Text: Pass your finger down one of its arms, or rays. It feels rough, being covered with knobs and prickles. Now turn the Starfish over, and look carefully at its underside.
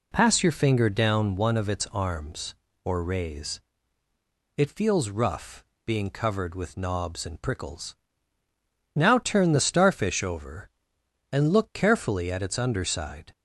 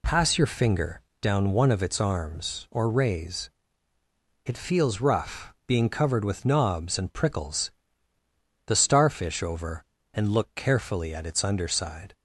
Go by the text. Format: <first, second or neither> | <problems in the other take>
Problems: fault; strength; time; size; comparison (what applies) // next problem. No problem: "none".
first | pauses between "finger" and "down"; slight; at 1.0 s; 0.18 s long // skips "Now turn"; at 8.1 s